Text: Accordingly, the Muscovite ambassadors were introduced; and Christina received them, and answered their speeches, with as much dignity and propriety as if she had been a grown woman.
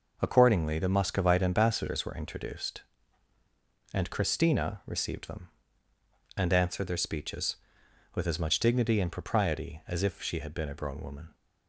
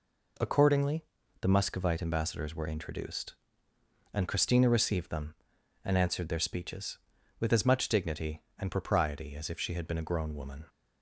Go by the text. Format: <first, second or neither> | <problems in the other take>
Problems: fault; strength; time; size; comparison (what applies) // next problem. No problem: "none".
neither | none